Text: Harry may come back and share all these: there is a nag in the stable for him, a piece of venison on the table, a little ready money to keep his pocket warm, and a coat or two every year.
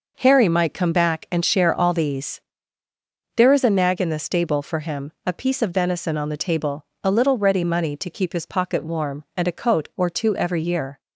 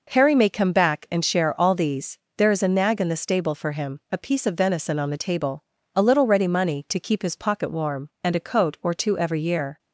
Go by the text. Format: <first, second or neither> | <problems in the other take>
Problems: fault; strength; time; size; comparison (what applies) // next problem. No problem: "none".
second | says "might" for "may"; at 0.4 s